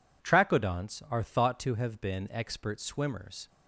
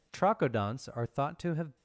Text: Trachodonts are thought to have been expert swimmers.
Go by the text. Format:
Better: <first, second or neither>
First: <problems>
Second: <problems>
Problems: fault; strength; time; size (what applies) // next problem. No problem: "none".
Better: first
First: none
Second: stops before "been expert swimmers"; at 1.7 s